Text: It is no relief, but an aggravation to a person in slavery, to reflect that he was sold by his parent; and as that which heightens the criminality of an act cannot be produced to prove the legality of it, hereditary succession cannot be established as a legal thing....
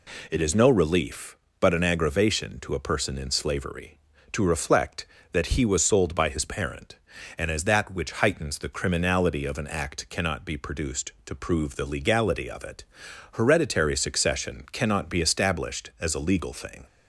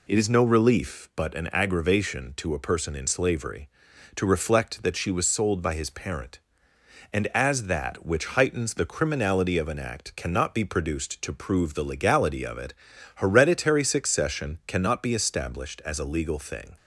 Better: first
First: none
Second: says "she" for "he"; at 4.9 s

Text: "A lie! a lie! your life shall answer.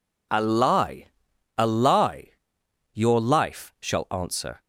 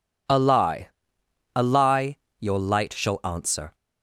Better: first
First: none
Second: says "light" for "life"; at 2.6 s

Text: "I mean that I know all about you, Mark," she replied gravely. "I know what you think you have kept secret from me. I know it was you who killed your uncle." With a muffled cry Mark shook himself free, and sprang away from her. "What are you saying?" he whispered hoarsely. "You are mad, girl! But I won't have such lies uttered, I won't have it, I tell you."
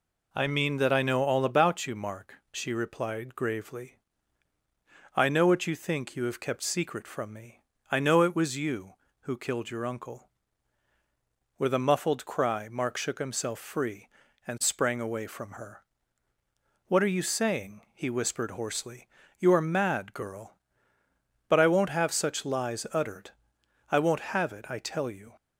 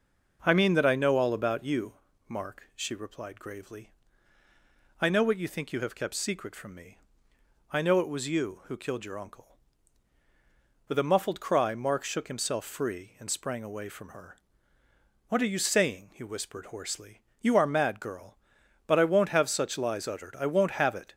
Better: first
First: none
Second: stops before "I tell you"; at 21.1 s

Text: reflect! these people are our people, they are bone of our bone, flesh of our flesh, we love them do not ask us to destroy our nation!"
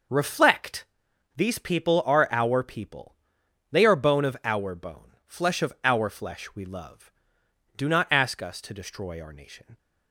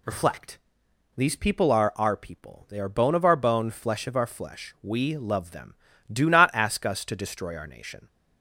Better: second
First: skips "them"; at 7.4 s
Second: none

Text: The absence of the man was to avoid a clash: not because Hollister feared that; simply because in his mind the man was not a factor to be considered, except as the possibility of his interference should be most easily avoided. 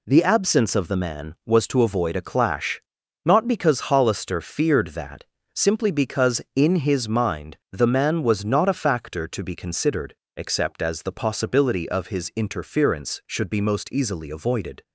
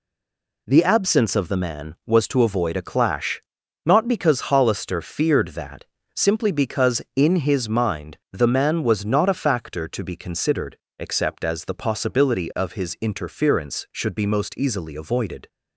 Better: first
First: none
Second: stays silent before the first word; slight; until 0.6 s; 0.6 s long

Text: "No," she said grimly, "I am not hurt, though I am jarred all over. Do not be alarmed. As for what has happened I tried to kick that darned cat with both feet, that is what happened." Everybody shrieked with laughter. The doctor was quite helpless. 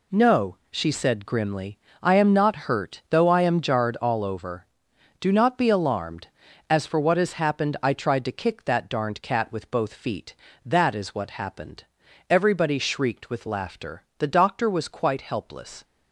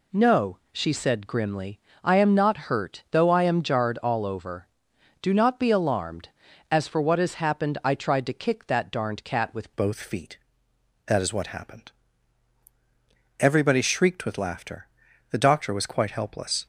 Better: first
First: none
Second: changes voice at "both"; from 9.7 s on; 6.9 s long

